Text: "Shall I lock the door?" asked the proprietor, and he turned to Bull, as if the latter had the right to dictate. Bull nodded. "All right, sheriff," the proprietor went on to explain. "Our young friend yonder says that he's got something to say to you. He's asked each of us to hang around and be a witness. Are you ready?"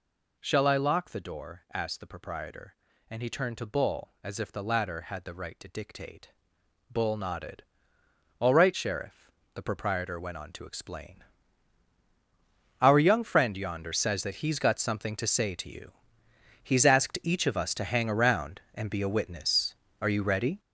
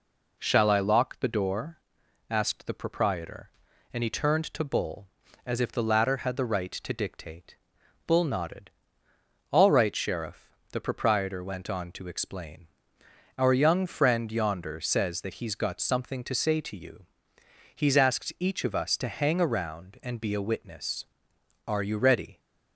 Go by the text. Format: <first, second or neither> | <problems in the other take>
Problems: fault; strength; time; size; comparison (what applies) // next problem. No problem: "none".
second | gets louder; strong; throughout; 8.5 dB